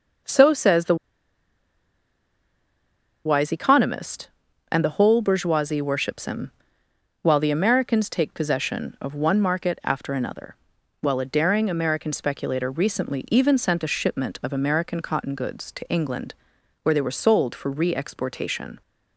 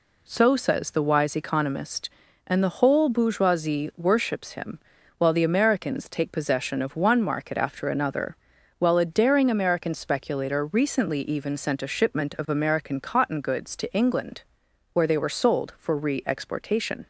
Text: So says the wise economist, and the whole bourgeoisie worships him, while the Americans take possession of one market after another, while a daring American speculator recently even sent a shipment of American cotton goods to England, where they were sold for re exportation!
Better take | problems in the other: second | pauses between "the" and "wise"; strong; at 0.9 s; 2.2 s long

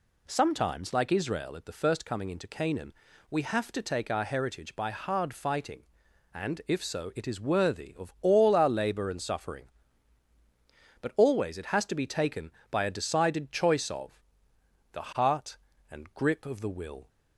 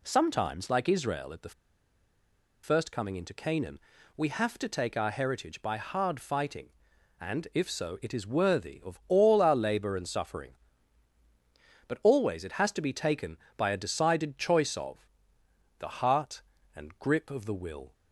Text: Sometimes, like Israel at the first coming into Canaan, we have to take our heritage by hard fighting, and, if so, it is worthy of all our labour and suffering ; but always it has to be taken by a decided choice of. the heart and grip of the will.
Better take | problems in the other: first | pauses between "the" and "first"; at 1.5 s; 1.1 s long

